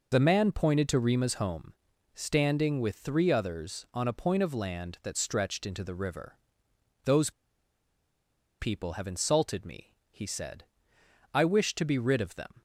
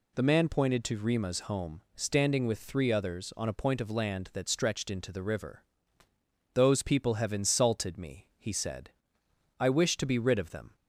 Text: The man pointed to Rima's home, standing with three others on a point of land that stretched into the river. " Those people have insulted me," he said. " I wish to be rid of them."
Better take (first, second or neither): second